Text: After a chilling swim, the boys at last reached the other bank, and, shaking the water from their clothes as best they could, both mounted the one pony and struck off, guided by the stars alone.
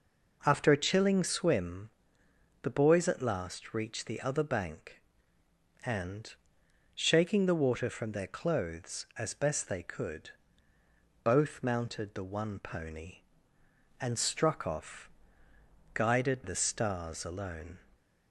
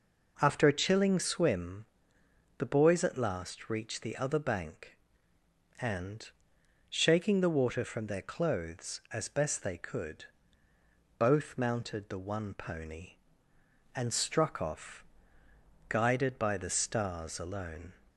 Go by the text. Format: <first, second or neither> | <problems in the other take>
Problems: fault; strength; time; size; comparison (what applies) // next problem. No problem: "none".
second | skips "by"; at 16.4 s